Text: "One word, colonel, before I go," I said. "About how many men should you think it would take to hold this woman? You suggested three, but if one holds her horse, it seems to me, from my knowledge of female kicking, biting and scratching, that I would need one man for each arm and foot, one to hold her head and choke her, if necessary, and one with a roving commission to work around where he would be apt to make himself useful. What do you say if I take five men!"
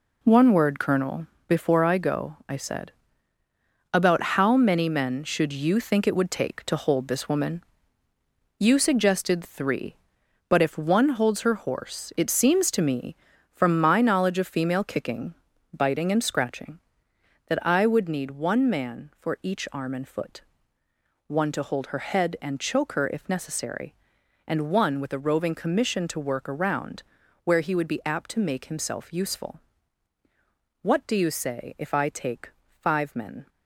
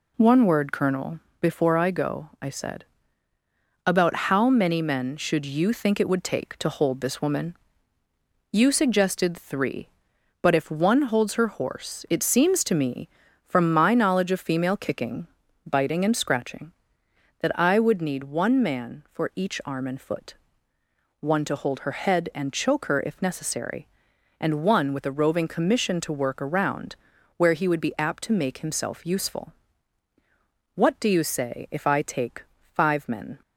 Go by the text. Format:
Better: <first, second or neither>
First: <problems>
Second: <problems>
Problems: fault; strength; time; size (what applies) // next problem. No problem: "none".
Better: second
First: gets quieter; strong; throughout; 8.5 dB // pauses between "About" and "how"; slight; at 4.2 s; 0.16 s long // pauses between "around" and "where"; at 27.0 s; 0.42 s long // pauses between "take" and "five"; slight; at 32.4 s; 0.30 s long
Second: pauses between "About" and "how"; slight; at 4.1 s; 0.16 s long // pauses between "around" and "where"; at 26.9 s; 0.42 s long // pauses between "take" and "five"; slight; at 32.4 s; 0.30 s long